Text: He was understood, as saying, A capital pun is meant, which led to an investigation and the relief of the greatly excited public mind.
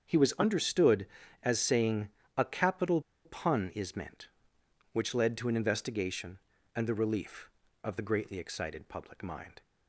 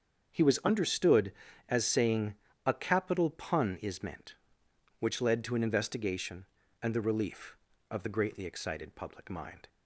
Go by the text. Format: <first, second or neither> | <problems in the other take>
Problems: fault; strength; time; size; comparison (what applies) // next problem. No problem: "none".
second | starts louder than the rest; until 1.0 s; 7 dB; also in the second // pauses between "capital" and "pun"; slight; at 3.0 s; 0.23 s long